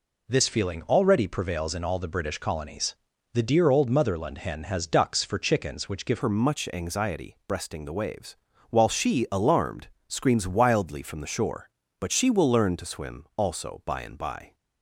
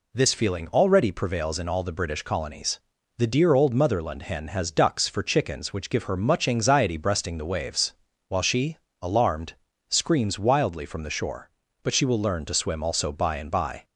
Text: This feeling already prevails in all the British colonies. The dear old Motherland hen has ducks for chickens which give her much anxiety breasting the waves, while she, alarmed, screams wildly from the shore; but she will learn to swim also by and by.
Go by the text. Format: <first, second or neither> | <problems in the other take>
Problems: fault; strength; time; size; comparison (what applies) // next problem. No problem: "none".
second | changes voice at "her"; from 6.2 s on; 8.3 s long